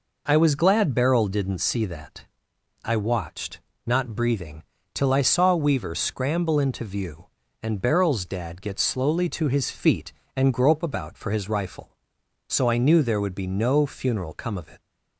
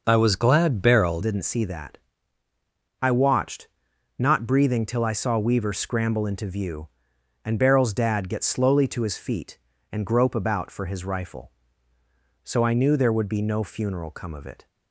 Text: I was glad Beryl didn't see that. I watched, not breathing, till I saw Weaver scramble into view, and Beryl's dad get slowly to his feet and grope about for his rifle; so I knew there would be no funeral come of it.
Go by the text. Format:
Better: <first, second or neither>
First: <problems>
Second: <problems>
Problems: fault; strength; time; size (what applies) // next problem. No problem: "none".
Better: first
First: none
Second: changes voice at "didn't"; from 1.2 s on; 13.4 s long